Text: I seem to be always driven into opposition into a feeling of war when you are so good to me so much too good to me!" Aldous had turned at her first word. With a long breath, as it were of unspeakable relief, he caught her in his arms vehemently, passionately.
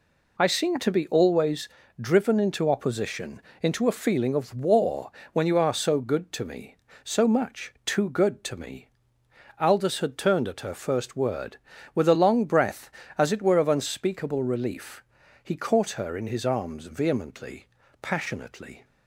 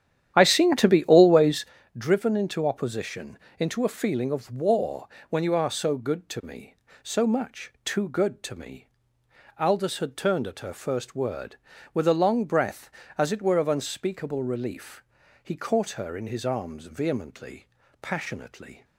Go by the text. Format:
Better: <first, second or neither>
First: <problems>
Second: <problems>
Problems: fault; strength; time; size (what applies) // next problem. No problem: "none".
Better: first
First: pauses between "always" and "driven"; slight; at 1.6 s; 0.32 s long // pauses between "opposition" and "into"; slight; at 3.3 s; 0.22 s long // pauses between "war" and "when"; slight; at 5.1 s; 0.20 s long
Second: starts louder than the rest; strong; until 1.9 s; 10 dB // pauses between "always" and "driven"; slight; at 1.6 s; 0.32 s long // pauses between "opposition" and "into"; slight; at 3.3 s; 0.22 s long // pauses between "war" and "when"; slight; at 5.0 s; 0.20 s long